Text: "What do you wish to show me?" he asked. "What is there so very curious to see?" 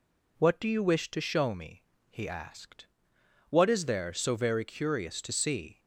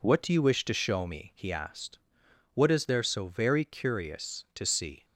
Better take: neither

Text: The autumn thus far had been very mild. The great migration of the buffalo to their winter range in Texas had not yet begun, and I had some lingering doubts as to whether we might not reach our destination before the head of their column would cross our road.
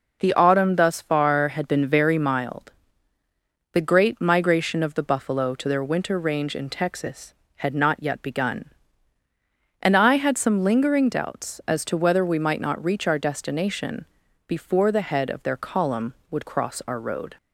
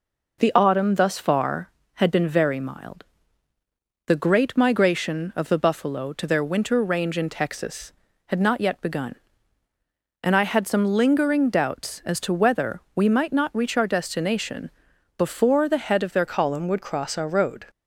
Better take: first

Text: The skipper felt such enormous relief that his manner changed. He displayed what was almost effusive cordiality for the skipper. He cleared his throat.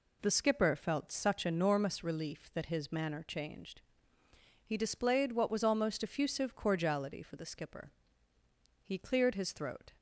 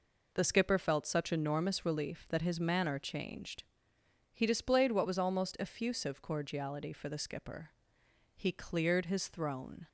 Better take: first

